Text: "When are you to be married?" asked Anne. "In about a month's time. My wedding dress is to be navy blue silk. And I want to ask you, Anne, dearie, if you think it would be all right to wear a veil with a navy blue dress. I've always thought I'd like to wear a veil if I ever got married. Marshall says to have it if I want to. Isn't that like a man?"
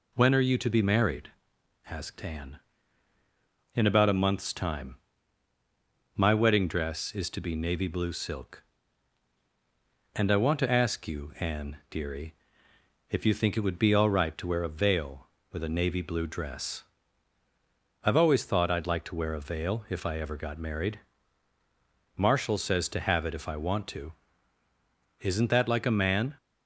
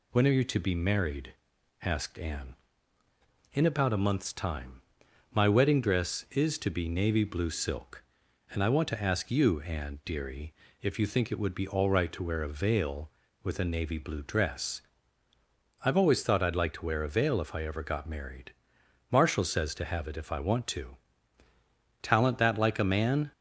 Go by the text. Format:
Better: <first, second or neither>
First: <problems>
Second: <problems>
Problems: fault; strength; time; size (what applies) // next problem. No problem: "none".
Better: first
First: none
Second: says "Talent" for "Isn't"; at 22.0 s